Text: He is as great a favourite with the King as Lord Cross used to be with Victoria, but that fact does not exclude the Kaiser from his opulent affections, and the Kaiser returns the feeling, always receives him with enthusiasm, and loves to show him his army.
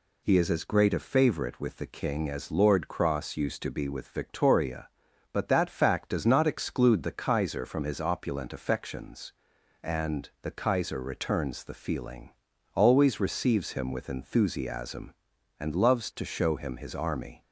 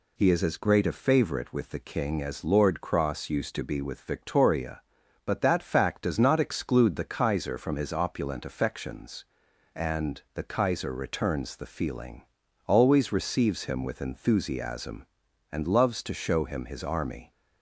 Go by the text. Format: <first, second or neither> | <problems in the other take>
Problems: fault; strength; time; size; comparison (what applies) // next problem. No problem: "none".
neither | none